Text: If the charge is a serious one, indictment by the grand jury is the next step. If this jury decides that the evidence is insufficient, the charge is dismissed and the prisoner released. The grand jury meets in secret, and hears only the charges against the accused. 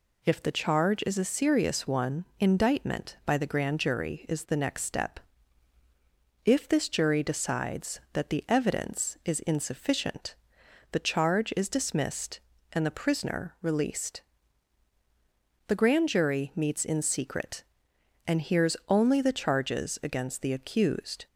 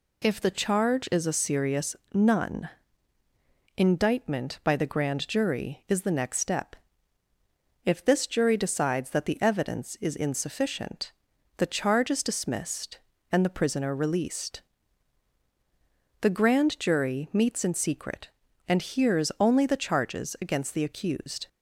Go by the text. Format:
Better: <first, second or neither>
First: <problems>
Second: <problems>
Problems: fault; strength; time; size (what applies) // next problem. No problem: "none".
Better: first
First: none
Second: says "none" for "one"; at 2.1 s